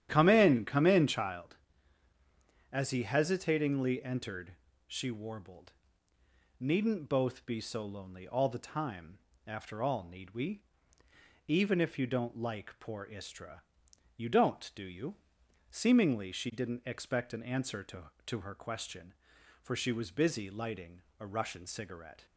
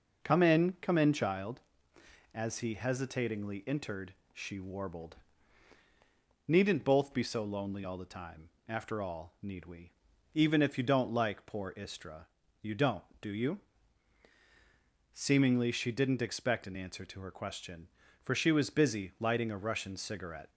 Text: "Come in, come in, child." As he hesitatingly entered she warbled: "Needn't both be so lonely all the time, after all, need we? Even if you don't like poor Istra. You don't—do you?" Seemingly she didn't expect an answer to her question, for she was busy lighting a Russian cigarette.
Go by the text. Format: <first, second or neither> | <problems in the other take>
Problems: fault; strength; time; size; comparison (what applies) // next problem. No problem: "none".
second | starts louder than the rest; strong; until 1.1 s; 11.5 dB // pauses between "entered" and "she"; slight; at 4.5 s; 0.32 s long; slight in the second // says "to" twice; at 18.2 s // pauses between "lighting" and "a"; slight; at 20.9 s; 0.22 s long